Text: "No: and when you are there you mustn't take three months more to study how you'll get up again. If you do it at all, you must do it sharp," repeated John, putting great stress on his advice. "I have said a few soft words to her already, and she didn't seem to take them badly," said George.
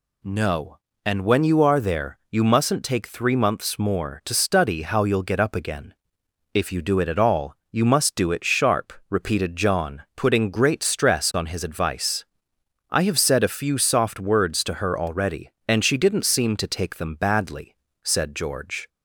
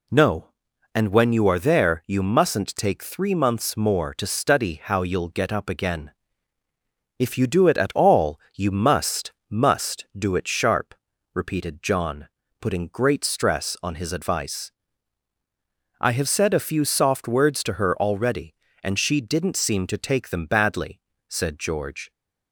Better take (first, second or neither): first